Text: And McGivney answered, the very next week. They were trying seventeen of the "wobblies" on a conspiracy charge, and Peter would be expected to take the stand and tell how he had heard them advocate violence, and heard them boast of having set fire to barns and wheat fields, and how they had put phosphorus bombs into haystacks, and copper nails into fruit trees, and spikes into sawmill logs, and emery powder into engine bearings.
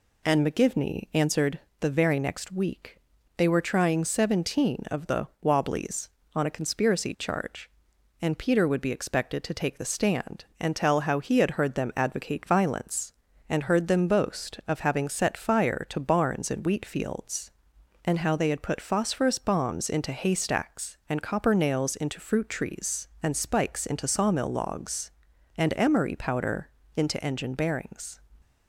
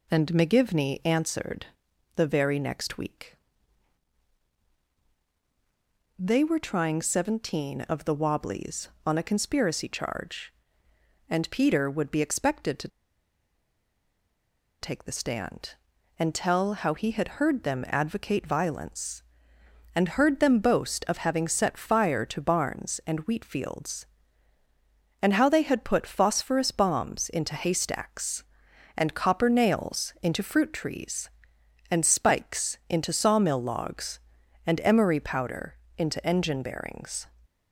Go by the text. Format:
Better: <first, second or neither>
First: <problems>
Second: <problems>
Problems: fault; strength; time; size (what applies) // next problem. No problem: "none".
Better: first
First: pauses between "powder" and "into"; slight; at 26.6 s; 0.26 s long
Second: pauses between "to" and "take"; strong; at 12.8 s; 1.9 s long // pauses between "powder" and "into"; slight; at 35.7 s; 0.22 s long